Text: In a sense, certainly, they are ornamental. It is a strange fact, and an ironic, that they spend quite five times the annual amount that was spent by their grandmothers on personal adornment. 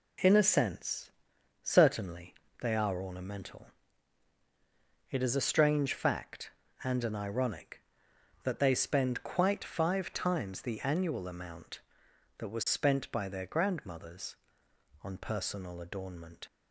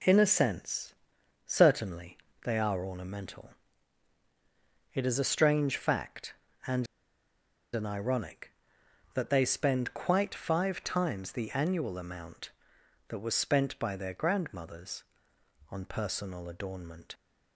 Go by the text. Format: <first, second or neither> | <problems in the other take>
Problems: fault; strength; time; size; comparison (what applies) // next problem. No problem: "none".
first | pauses between "and" and "an"; noticeable; at 6.8 s; 0.89 s long